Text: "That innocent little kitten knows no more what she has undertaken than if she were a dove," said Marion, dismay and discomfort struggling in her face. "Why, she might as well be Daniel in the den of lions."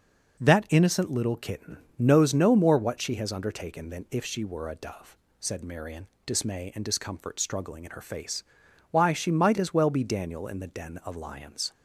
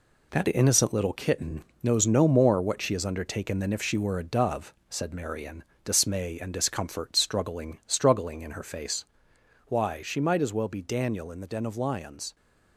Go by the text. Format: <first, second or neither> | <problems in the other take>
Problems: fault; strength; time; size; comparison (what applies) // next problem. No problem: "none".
first | pauses between "kitten" and "knows"; slight; at 1.6 s; 0.18 s long; slight in the first // says "struggling" twice; at 7.8 s